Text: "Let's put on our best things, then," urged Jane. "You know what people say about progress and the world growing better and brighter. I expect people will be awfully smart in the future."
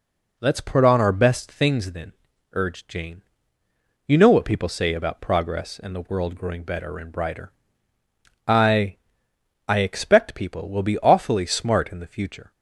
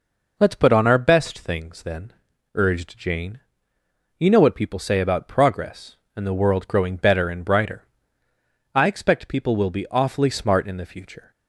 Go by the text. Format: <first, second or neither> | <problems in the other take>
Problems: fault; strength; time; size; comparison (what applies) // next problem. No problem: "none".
second | says "I" twice; at 9.6 s